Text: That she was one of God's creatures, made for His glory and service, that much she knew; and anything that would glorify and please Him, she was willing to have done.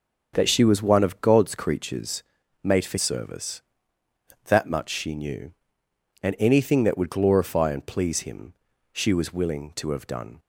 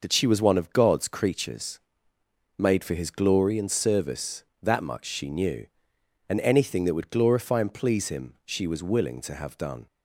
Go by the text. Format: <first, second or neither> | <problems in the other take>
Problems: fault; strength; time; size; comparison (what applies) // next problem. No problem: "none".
second | starts louder than the rest; until 1.3 s; 6.5 dB // skips "His glory and"; at 2.9 s